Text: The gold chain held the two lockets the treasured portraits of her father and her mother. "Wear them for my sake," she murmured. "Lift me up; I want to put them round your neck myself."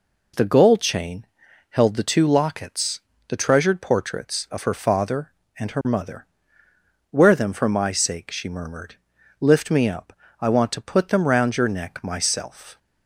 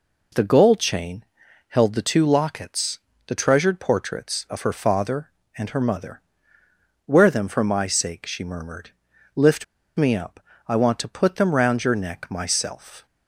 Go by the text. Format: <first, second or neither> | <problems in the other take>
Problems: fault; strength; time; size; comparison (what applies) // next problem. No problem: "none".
first | pauses between "chain" and "held"; at 1.2 s; 0.44 s long; also in the first // pauses between "lockets" and "the"; slight; at 2.9 s; 0.30 s long; slight in the first // pauses between "Lift" and "me"; slight; at 9.6 s; 0.34 s long